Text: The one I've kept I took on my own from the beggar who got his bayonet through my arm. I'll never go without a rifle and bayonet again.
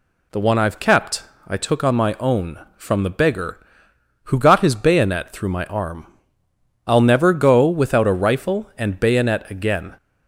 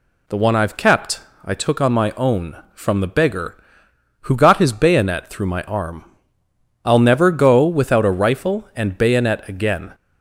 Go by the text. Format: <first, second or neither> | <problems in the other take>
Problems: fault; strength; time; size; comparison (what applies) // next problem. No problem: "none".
neither | pauses between "kept" and "I"; slight; the same in both